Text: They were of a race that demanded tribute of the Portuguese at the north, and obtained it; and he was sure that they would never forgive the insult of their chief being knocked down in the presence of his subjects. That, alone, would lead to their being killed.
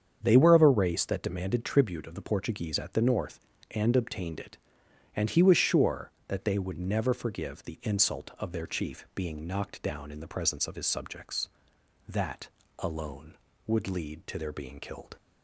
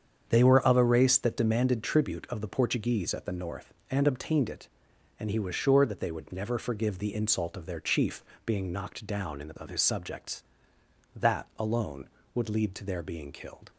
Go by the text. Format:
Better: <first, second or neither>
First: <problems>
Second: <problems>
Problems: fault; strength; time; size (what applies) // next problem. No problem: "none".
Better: first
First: starts louder than the rest; strong; until 1.2 s; 7.5 dB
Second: starts louder than the rest; strong; until 1.2 s; 7.5 dB // pauses between "chief" and "being"; slight; at 8.2 s; 0.20 s long // skips "presence"; at 9.5 s